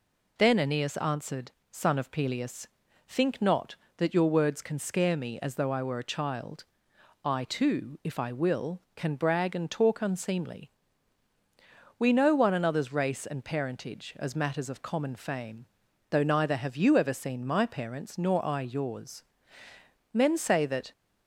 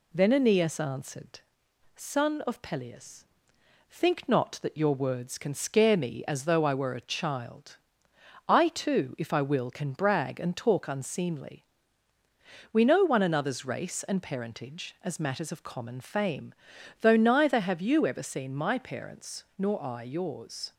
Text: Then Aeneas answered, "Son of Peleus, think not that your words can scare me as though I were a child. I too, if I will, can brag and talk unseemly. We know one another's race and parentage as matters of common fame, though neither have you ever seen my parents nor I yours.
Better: second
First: goes on to say "Men say that"; noticeable; from 20.1 s on; 0.80 s long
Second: none

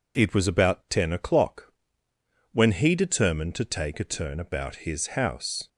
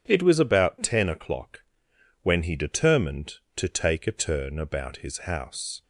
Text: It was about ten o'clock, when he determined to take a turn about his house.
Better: neither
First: none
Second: none

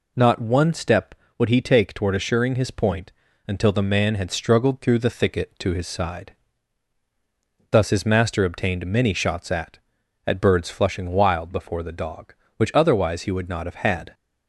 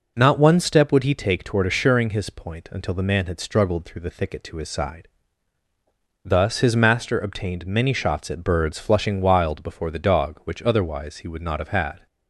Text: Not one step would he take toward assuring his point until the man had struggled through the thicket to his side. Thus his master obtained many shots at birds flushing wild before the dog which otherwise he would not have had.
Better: second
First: pauses between "point" and "until"; slight; at 3.1 s; 0.36 s long // says "at" twice; at 10.2 s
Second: none

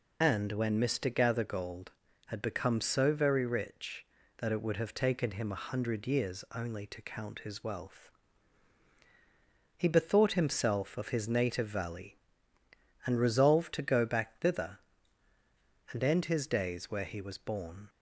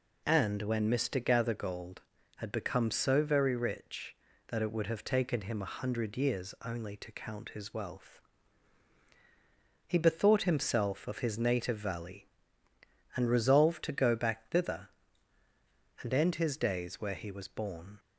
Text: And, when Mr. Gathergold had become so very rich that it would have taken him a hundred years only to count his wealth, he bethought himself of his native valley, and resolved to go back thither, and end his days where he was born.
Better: second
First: loses the start of "And"; at 0.2 s; 55 ms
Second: none

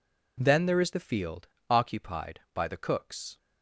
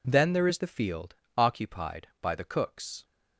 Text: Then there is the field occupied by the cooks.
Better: neither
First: pauses between "field" and "occupied"; slight; at 1.4 s; 0.22 s long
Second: pauses between "field" and "occupied"; slight; at 1.1 s; 0.22 s long

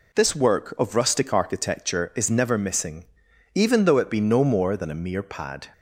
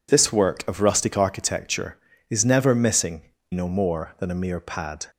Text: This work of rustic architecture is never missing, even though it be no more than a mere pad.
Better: first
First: none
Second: skips "even though it be"; at 3.3 s

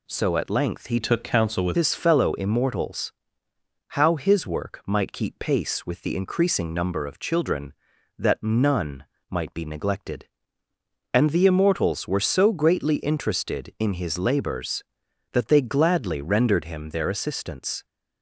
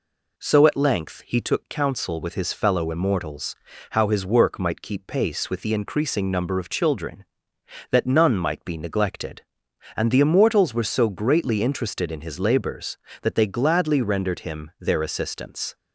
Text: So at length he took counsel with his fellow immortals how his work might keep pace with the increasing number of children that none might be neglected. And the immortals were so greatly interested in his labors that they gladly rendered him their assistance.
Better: second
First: changes voice from "took" to "with"; from 1.0 to 1.7 s; 0.7 s long // pauses between "immortals" and "how"; noticeable; at 3.1 s; 0.78 s long // pauses between "none" and "might"; slight; at 9.0 s; 0.26 s long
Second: pauses between "immortals" and "how"; slight; at 3.5 s; 0.34 s long

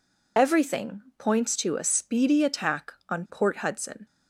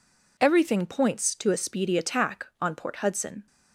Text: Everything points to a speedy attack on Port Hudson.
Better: second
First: loses the start of "Everything"; at 0.3 s; 50 ms // pauses between "Everything" and "points"; slight; at 1.0 s; 0.16 s long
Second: none

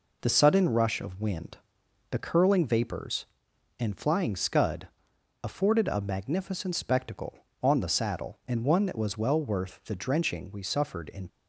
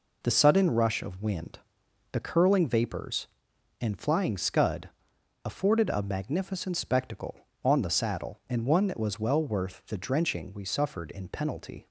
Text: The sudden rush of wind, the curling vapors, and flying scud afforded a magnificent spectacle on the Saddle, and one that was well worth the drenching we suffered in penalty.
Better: second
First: pauses between "scud" and "afforded"; noticeable; at 4.8 s; 0.56 s long // stops before "penalty"; at 11.2 s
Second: pauses between "scud" and "afforded"; noticeable; at 4.8 s; 0.56 s long

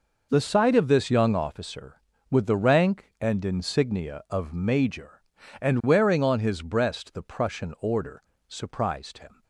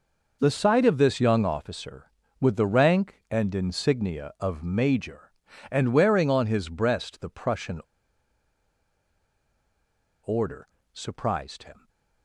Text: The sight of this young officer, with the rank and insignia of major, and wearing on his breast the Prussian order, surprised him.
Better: first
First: none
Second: pauses between "Prussian" and "order"; strong; at 7.8 s; 2.4 s long

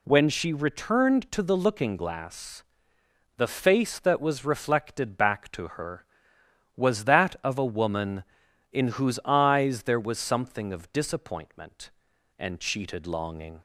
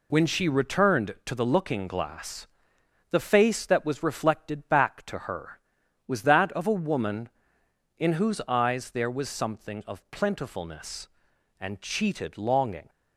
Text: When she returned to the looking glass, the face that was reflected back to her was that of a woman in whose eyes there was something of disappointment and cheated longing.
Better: first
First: none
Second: says "plentifulness" for "disappointment"; at 10.1 s

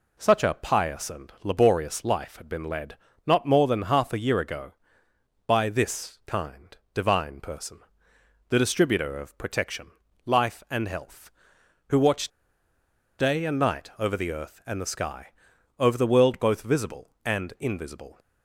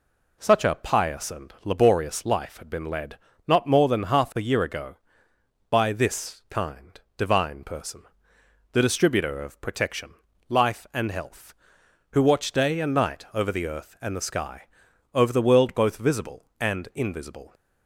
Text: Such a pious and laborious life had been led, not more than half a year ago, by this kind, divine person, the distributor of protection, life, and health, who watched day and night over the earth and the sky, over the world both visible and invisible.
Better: second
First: pauses between "watched" and "day"; noticeable; at 12.3 s; 0.90 s long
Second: none

